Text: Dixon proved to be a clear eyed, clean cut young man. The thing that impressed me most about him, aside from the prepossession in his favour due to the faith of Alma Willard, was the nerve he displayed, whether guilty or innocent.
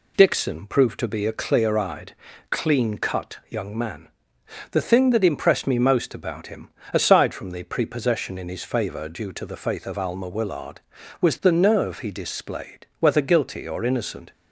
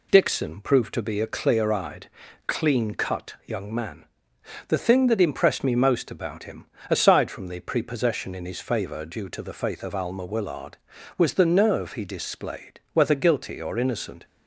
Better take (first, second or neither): neither